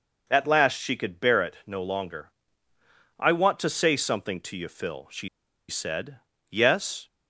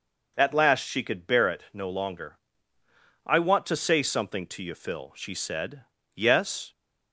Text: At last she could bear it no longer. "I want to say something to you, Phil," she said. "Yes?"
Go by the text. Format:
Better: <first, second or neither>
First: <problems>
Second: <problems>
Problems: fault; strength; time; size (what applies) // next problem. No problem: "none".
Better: second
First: pauses between "she" and "said"; at 5.2 s; 0.40 s long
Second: none